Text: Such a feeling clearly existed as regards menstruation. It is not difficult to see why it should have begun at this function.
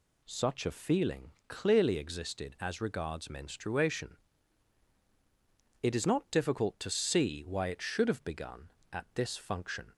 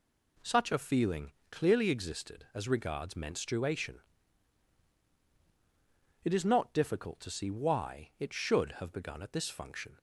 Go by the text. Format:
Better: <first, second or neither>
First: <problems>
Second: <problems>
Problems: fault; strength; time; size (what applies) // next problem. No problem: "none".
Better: neither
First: pauses between "feeling" and "clearly"; slight; at 1.3 s; 0.16 s long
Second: pauses between "feeling" and "clearly"; slight; at 1.3 s; 0.18 s long